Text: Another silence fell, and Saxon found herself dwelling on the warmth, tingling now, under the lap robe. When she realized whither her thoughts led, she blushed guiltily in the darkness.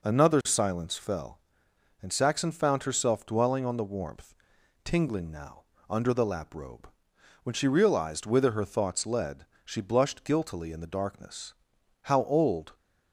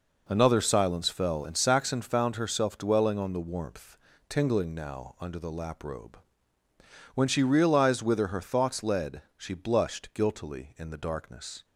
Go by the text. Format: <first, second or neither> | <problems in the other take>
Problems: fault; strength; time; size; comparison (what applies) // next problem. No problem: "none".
second | goes on to say "How old"; noticeable; from 12.0 s on; 0.72 s long